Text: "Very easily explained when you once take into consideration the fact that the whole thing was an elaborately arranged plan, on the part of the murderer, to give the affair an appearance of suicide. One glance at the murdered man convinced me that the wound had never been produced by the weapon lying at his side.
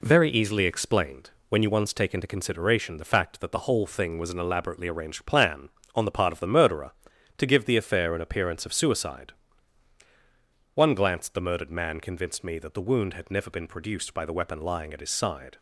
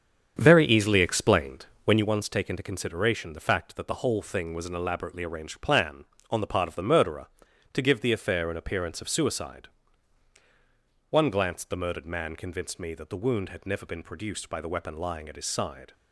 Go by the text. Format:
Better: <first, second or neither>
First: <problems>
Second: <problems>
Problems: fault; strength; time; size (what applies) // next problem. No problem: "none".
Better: first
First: pauses between "explained" and "when"; slight; at 1.2 s; 0.20 s long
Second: starts louder than the rest; strong; until 2.0 s; 8 dB // pauses between "explained" and "when"; slight; at 1.6 s; 0.20 s long